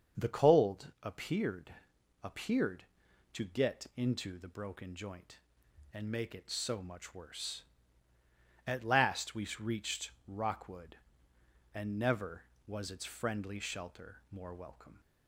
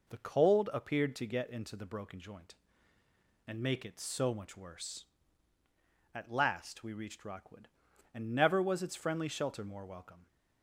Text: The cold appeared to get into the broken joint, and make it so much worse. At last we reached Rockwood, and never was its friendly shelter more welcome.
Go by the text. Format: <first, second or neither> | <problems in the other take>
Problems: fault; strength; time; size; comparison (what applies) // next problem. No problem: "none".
second | starts louder than the rest; until 1.2 s; 7 dB // says "appeared" twice; at 2.2 s